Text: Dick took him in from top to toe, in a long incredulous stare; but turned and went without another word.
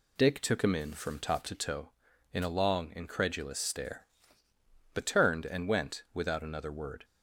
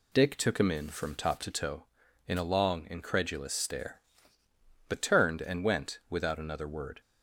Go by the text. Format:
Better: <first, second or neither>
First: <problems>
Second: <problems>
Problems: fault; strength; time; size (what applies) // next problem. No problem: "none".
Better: neither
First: none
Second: none